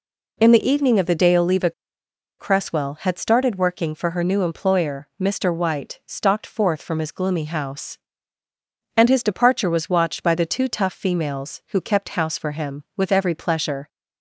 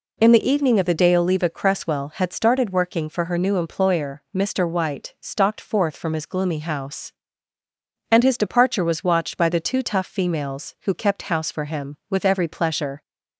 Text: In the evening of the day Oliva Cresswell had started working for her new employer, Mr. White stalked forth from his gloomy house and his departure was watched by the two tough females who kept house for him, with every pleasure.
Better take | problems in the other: second | pauses between "Oliva" and "Cresswell"; noticeable; at 1.7 s; 0.67 s long

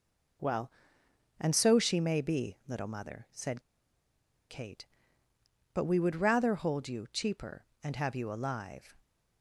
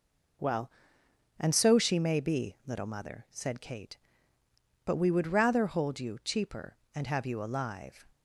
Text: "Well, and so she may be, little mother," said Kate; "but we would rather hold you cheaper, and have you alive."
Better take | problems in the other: second | pauses between "said" and "Kate"; noticeable; at 3.6 s; 0.88 s long

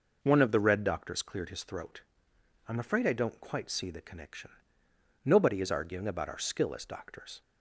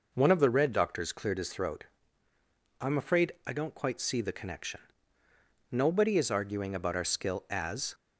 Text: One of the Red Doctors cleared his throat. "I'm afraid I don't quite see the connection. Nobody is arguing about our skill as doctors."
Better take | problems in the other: first | stops before "doctors"; at 7.9 s

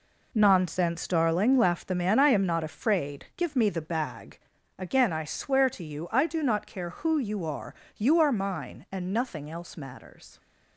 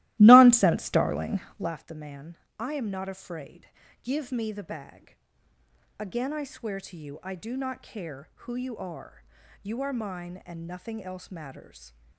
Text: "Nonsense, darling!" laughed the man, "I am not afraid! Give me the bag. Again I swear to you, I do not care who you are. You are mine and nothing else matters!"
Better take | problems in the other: first | starts louder than the rest; strong; until 1.7 s; 16.5 dB

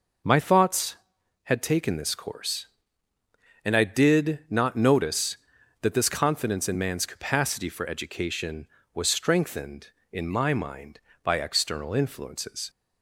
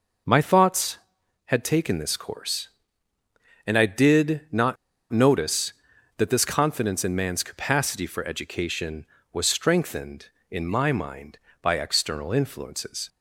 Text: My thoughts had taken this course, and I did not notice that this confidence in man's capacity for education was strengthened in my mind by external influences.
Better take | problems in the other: first | pauses between "not" and "notice"; at 4.7 s; 0.36 s long

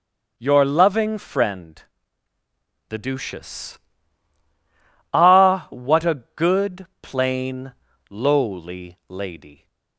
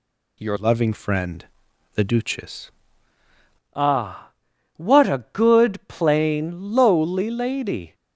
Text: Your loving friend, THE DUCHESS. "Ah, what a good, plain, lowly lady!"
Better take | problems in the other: first | changes voice from "loving" to "DUCHESS"; from 0.5 to 2.6 s; 2.1 s long

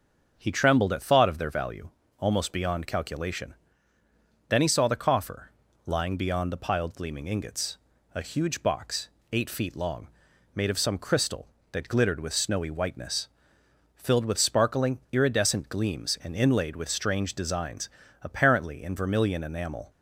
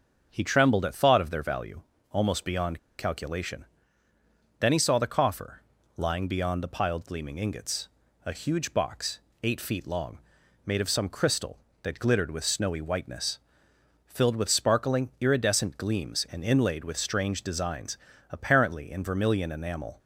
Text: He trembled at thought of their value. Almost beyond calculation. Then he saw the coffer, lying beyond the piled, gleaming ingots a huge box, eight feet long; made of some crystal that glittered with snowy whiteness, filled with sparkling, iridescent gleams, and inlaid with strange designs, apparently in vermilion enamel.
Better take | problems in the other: first | starts louder than the rest; until 1.3 s; 7 dB; also in the first // pauses between "beyond" and "calculation"; slight; at 2.7 s; 0.18 s long // pauses between "ingots" and "a"; at 7.8 s; 0.38 s long; also in the first

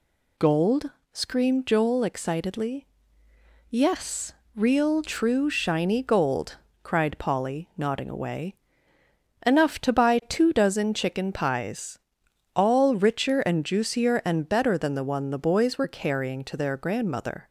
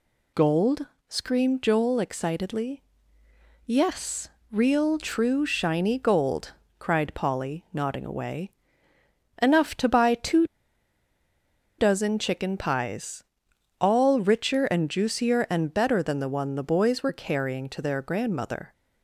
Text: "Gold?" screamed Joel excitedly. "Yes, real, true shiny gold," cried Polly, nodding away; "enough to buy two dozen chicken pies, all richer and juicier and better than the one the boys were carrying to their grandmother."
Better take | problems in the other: first | pauses between "two" and "dozen"; strong; at 10.4 s; 1.3 s long

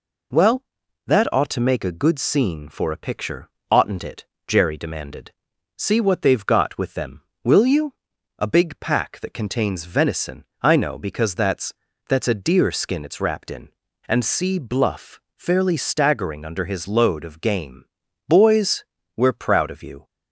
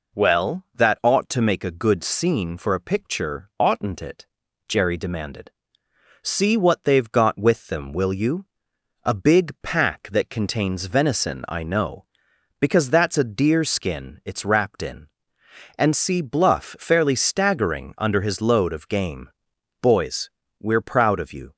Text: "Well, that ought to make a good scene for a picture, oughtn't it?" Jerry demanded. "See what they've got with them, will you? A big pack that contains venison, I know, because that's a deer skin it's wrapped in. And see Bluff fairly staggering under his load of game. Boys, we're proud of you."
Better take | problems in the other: second | says "that's" twice; at 12.0 s // pauses between "Bluff" and "fairly"; slight; at 15.1 s; 0.16 s long

